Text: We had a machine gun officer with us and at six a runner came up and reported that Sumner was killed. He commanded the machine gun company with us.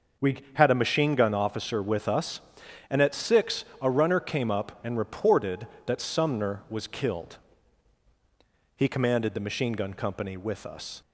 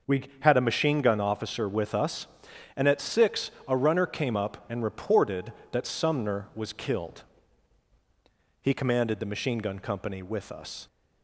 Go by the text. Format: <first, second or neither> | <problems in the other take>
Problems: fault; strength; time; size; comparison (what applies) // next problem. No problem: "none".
neither | starts louder than the rest; the same in both // pauses between "six" and "a"; slight; the same in both